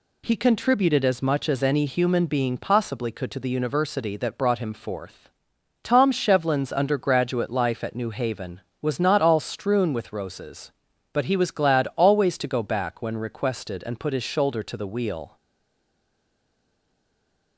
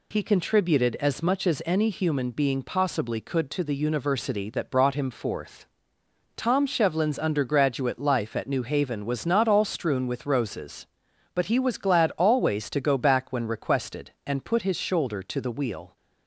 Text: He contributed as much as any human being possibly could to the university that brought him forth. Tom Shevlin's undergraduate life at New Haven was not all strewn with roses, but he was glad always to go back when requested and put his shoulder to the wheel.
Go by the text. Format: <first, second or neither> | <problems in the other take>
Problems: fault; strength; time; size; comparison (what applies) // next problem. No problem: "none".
second | stays silent after the last word; from 15.3 s on; 2.2 s long